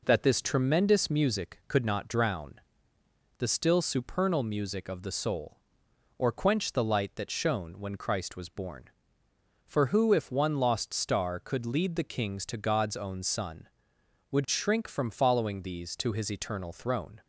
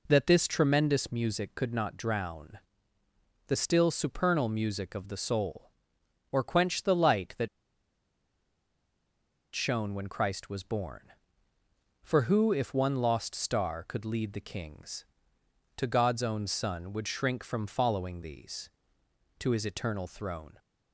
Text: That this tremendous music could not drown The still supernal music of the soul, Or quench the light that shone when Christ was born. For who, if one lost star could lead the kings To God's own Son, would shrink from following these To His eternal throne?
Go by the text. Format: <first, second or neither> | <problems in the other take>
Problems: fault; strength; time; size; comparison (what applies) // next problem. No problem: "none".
first | pauses between "drown" and "The"; noticeable; at 2.5 s; 0.90 s long; noticeable in the first // pauses between "that" and "shone"; strong; at 7.4 s; 2.0 s long